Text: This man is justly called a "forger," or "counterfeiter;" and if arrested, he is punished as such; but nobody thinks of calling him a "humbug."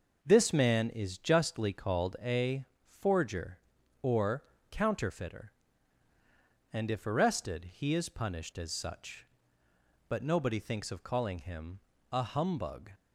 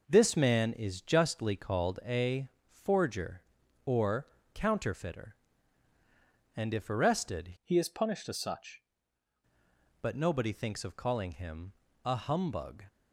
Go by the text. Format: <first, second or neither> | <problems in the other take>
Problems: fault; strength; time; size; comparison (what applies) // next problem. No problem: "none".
first | pauses between "a" and "forger"; slight; at 2.4 s; 0.20 s long; slight in the first // pauses between "or" and "counterfeiter"; slight; at 4.2 s; 0.26 s long; slight in the first // changes voice from "he" to "such"; from 7.6 to 8.8 s; 1.2 s long // pauses between "him" and "a"; slight; at 11.7 s; 0.28 s long; slight in the first